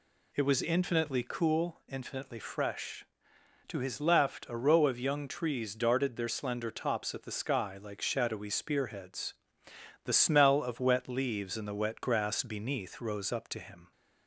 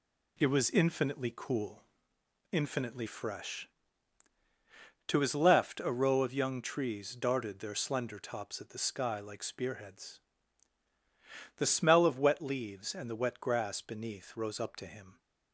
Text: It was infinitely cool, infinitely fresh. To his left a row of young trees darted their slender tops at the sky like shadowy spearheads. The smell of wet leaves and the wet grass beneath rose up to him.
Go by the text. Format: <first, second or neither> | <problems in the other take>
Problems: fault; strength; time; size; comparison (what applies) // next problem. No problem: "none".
first | skips "shadowy"; at 9.4 s